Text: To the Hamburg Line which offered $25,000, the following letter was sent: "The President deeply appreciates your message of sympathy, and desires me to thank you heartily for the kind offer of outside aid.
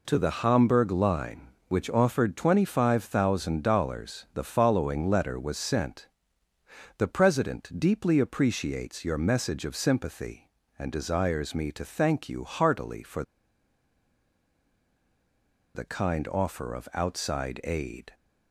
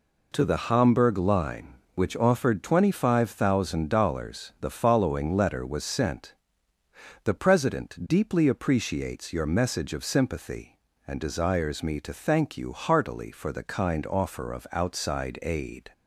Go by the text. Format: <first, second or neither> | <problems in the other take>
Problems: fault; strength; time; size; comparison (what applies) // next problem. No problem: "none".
second | pauses between "for" and "the"; strong; at 13.2 s; 2.5 s long